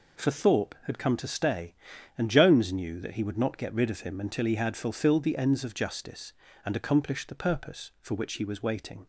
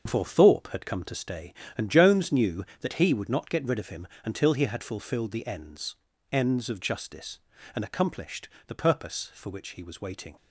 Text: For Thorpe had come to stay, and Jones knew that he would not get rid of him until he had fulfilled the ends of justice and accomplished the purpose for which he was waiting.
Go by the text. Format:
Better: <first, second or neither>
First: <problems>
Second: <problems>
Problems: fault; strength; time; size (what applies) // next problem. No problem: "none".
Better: first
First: none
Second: starts louder than the rest; until 1.0 s; 7 dB // pauses between "him" and "until"; slight; at 4.0 s; 0.18 s long // says "ends" twice; at 6.3 s // pauses between "accomplished" and "the"; slight; at 8.4 s; 0.18 s long